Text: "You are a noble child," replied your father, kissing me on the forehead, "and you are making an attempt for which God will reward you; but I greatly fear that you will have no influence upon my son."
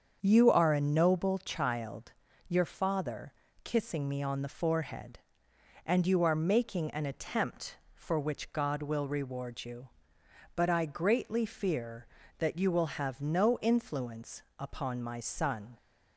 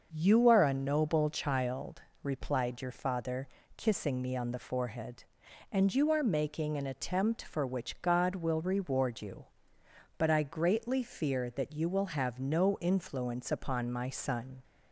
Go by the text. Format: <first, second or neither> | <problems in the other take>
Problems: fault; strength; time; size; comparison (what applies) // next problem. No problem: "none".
second | starts louder than the rest; until 1.2 s; 7 dB; noticeable in the second // skips "replied"; at 2.2 s // pauses between "influence" and "upon"; slight; at 14.4 s; 0.18 s long